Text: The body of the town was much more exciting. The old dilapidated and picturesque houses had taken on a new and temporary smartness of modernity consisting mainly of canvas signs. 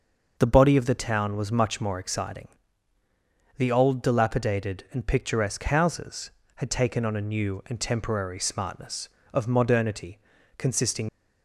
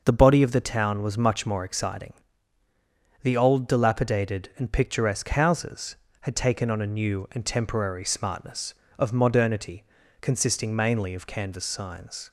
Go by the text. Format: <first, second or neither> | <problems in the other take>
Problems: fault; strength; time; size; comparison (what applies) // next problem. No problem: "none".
second | pauses between "modernity" and "consisting"; at 10.1 s; 0.38 s long; also in the second // stops before "mainly of canvas signs"; at 11.0 s